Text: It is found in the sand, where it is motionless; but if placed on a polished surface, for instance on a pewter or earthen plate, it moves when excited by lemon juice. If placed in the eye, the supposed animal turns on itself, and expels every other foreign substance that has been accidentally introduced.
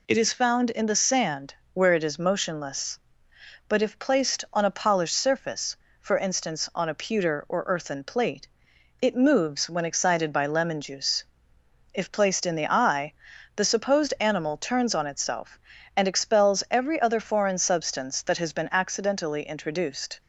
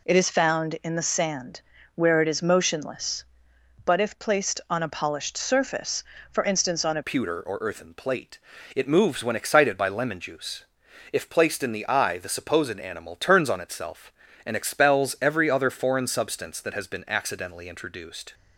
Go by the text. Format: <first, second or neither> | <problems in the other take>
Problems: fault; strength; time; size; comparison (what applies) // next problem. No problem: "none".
first | changes voice at "pewter"; from 7.0 s on; 11.3 s long